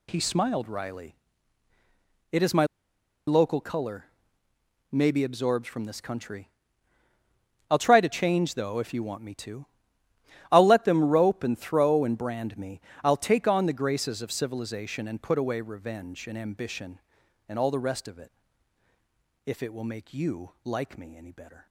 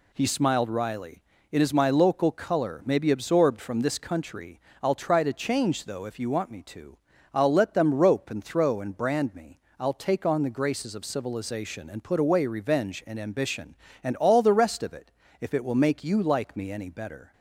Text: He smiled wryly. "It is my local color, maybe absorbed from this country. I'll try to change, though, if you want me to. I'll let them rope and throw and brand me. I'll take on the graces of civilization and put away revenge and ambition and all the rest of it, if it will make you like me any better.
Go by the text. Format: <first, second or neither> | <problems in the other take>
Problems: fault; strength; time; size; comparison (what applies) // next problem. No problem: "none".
second | pauses between "my" and "local"; noticeable; at 2.6 s; 0.61 s long